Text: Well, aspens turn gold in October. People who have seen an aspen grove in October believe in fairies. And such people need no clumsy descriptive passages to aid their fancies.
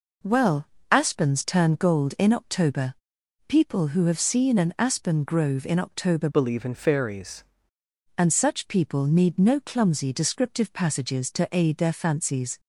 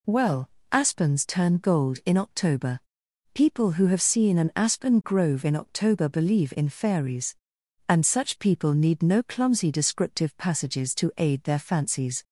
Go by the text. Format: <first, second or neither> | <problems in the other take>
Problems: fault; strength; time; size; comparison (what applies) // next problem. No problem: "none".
second | changes voice from "believe" to "fairies"; from 6.3 to 7.4 s; 1.1 s long